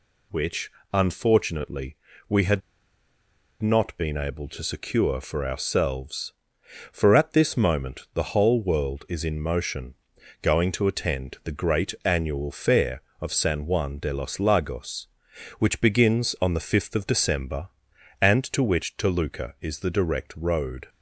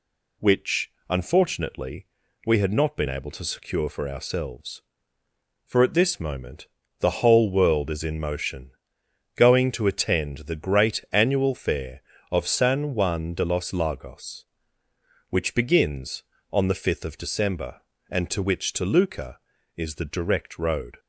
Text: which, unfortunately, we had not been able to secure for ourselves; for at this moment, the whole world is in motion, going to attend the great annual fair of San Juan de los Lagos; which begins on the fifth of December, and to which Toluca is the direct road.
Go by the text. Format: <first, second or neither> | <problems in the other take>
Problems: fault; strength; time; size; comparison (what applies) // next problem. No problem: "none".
second | pauses between "had" and "not"; at 2.6 s; 1.0 s long